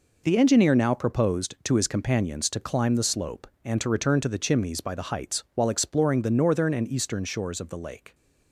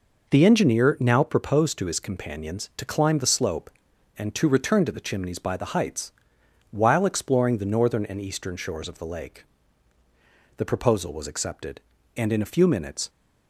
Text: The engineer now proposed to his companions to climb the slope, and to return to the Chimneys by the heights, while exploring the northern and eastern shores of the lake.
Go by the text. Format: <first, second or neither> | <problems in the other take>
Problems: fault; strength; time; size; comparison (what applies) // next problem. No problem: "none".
first | goes on to say "The proposal was accepted and in a few minutes"; strong; from 10.5 s on; 2.5 s long